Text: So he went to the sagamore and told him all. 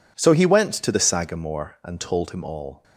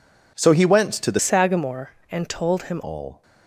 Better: first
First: none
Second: changes voice from "sagamore" to "him"; from 1.1 to 2.8 s; 1.7 s long

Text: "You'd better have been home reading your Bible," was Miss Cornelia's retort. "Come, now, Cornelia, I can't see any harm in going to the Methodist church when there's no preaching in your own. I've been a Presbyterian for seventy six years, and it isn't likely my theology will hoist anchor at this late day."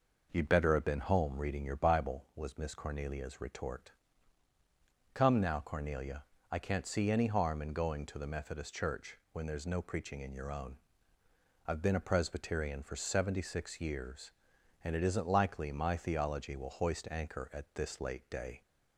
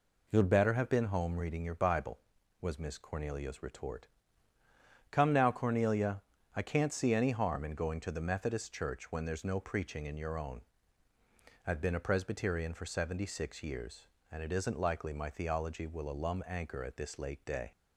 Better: first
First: none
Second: says "alum" for "hoist"; at 16.0 s

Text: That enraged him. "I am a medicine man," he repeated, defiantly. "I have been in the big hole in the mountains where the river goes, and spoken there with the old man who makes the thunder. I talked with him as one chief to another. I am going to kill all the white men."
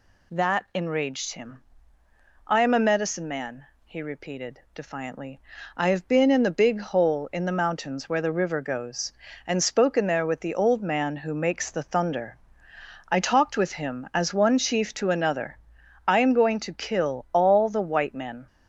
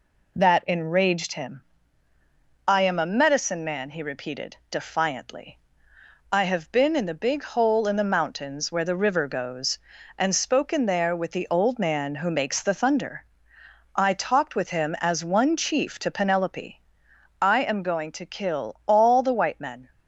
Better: first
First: none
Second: says "penelope" for "another"; at 16.1 s

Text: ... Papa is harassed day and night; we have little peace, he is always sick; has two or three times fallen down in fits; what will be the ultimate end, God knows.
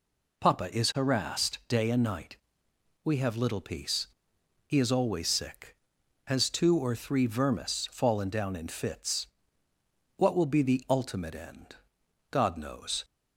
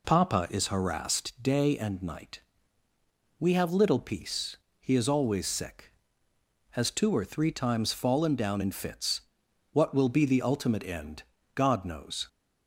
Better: second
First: says "vermis" for "times"; at 7.2 s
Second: none

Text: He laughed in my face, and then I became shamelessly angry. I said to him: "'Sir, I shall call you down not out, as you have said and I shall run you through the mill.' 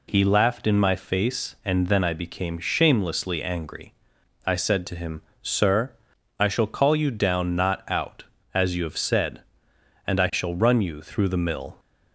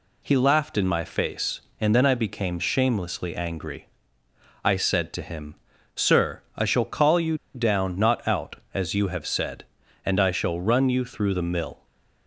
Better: first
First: none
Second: pauses between "you" and "down"; slight; at 7.3 s; 0.18 s long

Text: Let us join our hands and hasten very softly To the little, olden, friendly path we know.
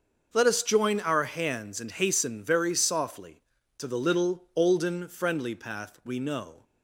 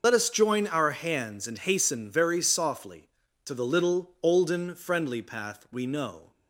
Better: first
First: starts louder than the rest; until 1.3 s; 6.5 dB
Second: loses the start of "Let"; at 0.0 s; 40 ms // starts louder than the rest; noticeable; until 1.0 s; 6 dB

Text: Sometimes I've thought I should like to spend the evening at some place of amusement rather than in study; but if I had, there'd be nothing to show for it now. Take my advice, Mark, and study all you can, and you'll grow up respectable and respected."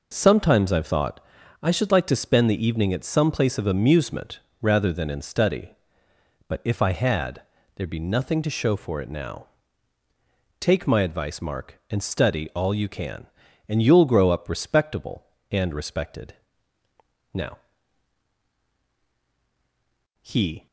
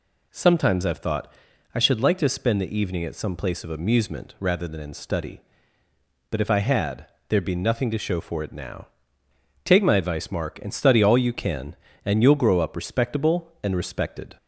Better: second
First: pauses between "thought" and "I"; at 1.2 s; 0.42 s long // pauses between "amusement" and "rather"; slight; at 4.4 s; 0.20 s long // goes on to say "Now he"; strong; from 17.3 s on; 3.3 s long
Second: pauses between "thought" and "I"; at 1.3 s; 0.44 s long

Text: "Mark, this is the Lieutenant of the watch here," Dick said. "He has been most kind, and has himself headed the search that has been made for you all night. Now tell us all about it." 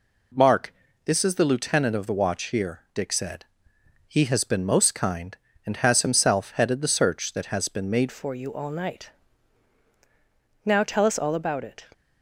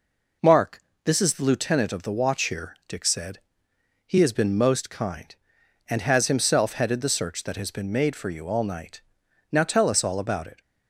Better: second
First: changes voice at "for"; from 8.1 s on; 3.7 s long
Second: none

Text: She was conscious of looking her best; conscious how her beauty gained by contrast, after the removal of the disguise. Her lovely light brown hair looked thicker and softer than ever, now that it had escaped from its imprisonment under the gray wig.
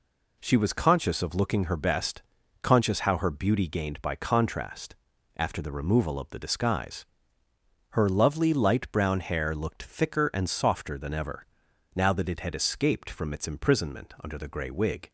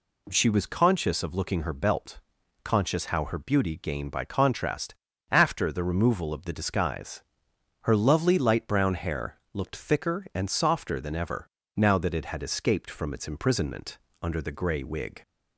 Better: first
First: none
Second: says "belt" for "best"; at 1.7 s // pauses between "imprisonment" and "under"; slight; at 13.9 s; 0.24 s long

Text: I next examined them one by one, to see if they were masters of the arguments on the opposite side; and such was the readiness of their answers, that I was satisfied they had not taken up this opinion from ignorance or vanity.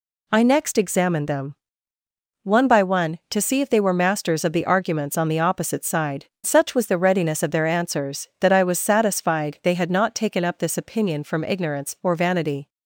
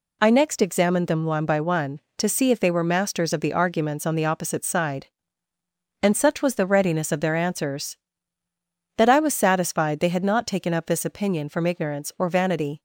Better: second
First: pauses between "them" and "one"; noticeable; at 1.5 s; 0.88 s long // skips "and"; at 6.3 s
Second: none

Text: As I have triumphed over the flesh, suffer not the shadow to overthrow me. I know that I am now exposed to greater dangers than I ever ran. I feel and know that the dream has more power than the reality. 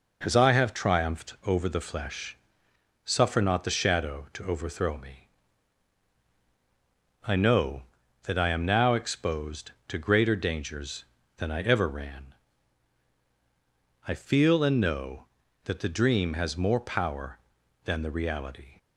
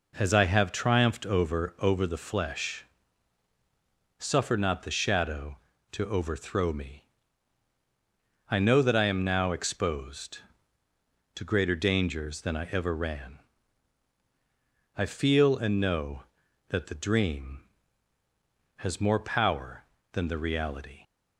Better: first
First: none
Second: says "over" twice; at 1.8 s

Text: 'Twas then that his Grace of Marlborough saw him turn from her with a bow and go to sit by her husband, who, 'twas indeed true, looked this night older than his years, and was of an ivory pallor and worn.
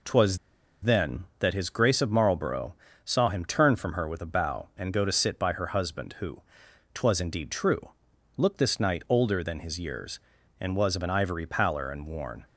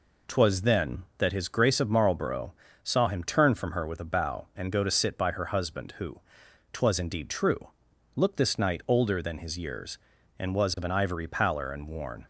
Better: second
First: pauses between "Twas" and "then"; at 0.3 s; 0.44 s long // pauses between "Marlborough" and "saw"; slight; at 2.7 s; 0.28 s long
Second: pauses between "Marlborough" and "saw"; slight; at 2.5 s; 0.28 s long

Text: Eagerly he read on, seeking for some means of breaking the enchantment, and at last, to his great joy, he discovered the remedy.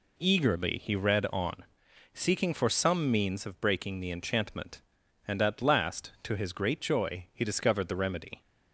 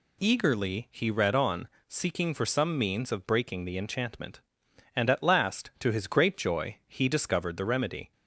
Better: neither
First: none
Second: none

